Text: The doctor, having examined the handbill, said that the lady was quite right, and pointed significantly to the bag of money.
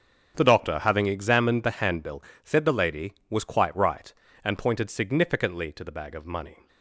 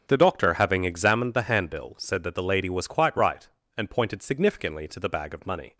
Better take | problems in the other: second | starts louder than the rest; strong; until 1.3 s; 7 dB; also in the second // skips "that"; at 2.6 s

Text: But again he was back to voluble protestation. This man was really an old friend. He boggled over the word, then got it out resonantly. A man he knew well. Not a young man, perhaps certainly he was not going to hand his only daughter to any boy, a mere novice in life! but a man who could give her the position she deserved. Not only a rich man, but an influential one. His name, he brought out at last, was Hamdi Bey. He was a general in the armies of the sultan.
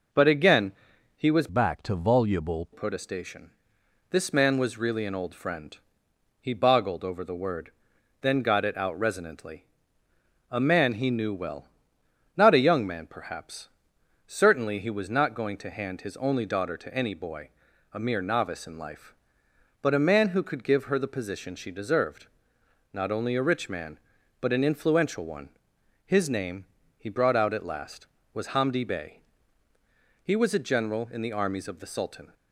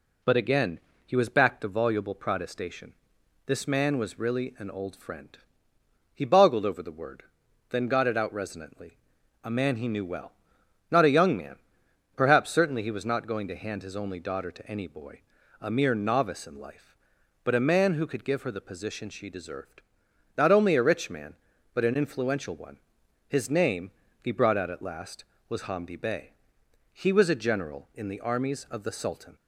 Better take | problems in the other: second | pauses between "again" and "he"; at 0.7 s; 0.42 s long; slight in the second // changes voice from "back" to "voluble"; from 1.4 to 2.6 s; 1.2 s long // pauses between "perhaps" and "certainly"; noticeable; at 13.6 s; 0.56 s long

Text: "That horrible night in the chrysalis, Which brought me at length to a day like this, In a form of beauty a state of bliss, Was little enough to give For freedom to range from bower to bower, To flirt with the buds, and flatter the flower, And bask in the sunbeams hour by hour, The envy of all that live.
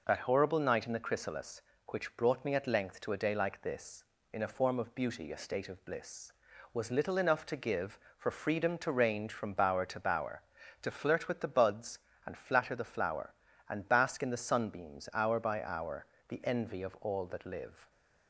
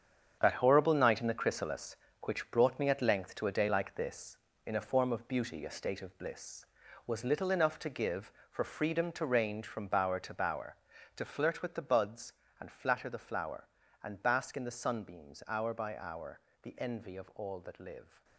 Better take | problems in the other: first | gets quieter; strong; throughout; 10 dB

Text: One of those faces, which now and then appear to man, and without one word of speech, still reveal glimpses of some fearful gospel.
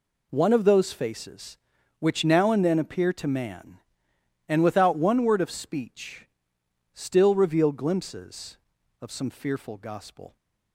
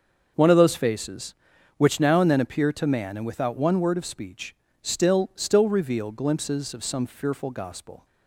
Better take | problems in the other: first | starts louder than the rest; until 1.7 s; 6.5 dB // says "still" twice; at 5.3 s

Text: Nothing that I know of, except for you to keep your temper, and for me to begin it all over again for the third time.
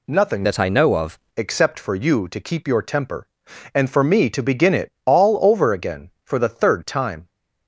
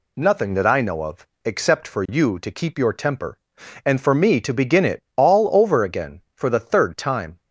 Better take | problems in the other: second | changes voice from "that" to "of"; from 0.4 to 1.1 s; 0.7 s long

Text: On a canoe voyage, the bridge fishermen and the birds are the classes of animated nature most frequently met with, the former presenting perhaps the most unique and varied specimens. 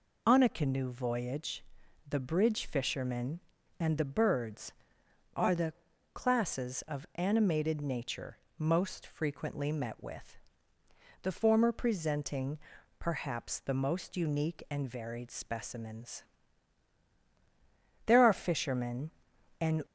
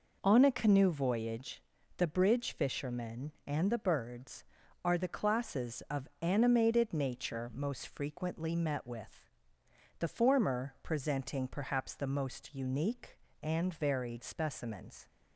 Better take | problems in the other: second | pauses between "the" and "classes"; at 5.7 s; 0.40 s long // pauses between "nature" and "most"; slight; at 8.3 s; 0.22 s long // pauses between "presenting" and "perhaps"; at 12.5 s; 0.40 s long // goes on to say "There are fishermen and"; strong; from 18.0 s on; 1.7 s long

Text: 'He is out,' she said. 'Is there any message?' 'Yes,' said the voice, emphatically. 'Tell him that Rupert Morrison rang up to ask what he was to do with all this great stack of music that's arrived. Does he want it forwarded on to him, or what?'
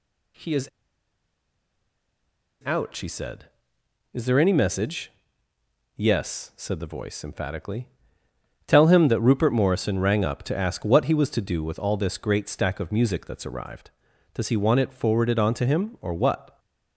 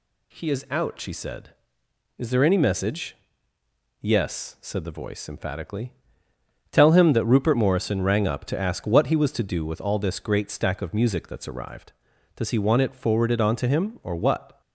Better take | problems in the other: second | pauses between "is" and "out"; strong; at 0.6 s; 1.9 s long

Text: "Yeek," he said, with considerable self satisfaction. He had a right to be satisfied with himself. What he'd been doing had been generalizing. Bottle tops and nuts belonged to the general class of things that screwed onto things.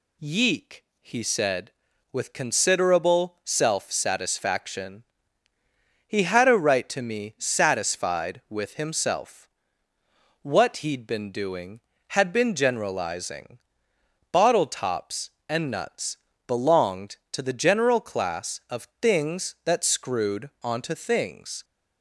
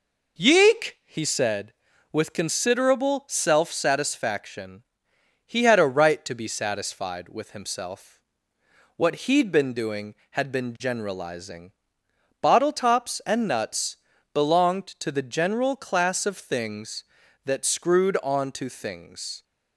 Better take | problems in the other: second | says "me" for "be"; at 7.0 s // pauses between "nuts" and "belonged"; slight; at 16.1 s; 0.30 s long; slight in the second

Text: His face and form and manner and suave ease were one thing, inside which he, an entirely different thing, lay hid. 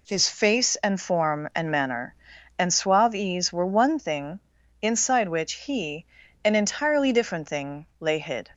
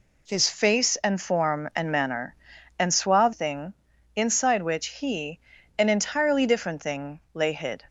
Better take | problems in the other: first | skips "ease were one"; at 3.3 s

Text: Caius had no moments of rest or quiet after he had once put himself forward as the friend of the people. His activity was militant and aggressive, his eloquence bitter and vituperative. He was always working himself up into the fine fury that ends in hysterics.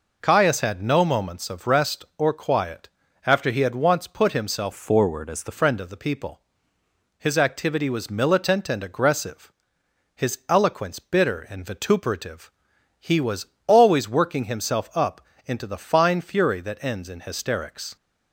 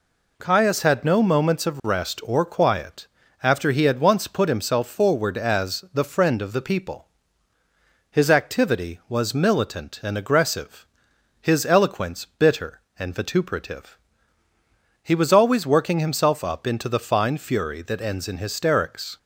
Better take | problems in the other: second | pauses between "quiet" and "after"; slight; at 2.8 s; 0.36 s long; slight in the second // changes voice from "forward" to "the"; from 4.7 to 5.5 s; 0.8 s long // pauses between "was" and "always"; slight; at 13.4 s; 0.18 s long // pauses between "up" and "into"; slight; at 15.2 s; 0.24 s long

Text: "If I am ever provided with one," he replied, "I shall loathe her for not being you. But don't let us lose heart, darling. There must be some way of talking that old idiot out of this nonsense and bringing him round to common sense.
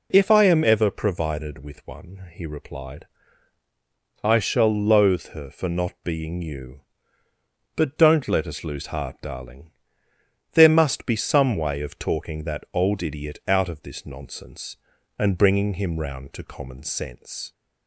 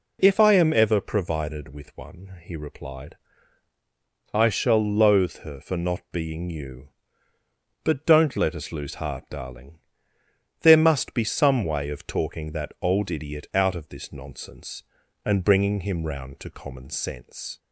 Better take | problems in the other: neither | none

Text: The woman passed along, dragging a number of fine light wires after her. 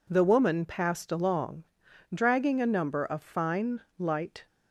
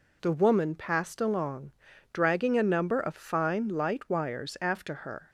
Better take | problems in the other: second | pauses between "fine" and "light"; slight; at 3.8 s; 0.16 s long // stops before "wires after her"; at 4.4 s

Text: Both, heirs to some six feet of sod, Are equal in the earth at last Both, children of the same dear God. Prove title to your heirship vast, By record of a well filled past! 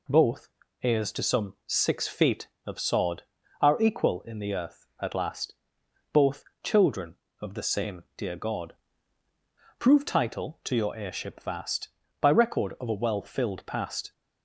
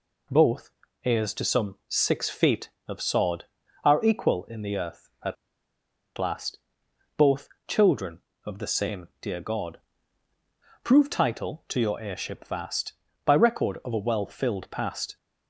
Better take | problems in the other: first | pauses between "at" and "last"; noticeable; at 5.3 s; 0.83 s long // pauses between "last" and "Both"; noticeable; at 6.5 s; 0.58 s long; noticeable in the first

